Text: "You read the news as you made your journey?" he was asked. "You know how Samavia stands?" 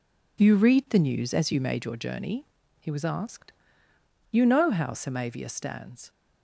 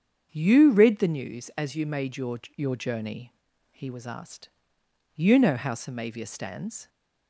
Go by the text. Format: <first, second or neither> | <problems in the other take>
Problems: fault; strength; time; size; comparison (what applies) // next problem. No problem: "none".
first | starts louder than the rest; strong; until 1.3 s; 7.5 dB // says "your" twice; at 2.5 s